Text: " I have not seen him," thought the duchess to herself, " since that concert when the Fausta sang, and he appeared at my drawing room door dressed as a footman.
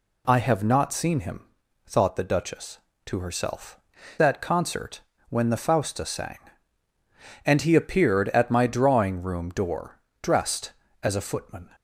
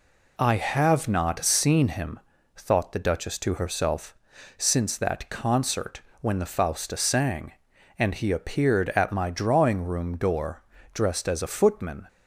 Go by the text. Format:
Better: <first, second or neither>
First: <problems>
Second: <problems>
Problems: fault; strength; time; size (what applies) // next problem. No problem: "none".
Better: second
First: skips "since"; at 4.1 s // pauses between "concert" and "when"; slight; at 5.0 s; 0.30 s long // pauses between "door" and "dressed"; slight; at 9.9 s; 0.22 s long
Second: pauses between "concert" and "when"; slight; at 6.0 s; 0.20 s long // pauses between "door" and "dressed"; slight; at 10.6 s; 0.32 s long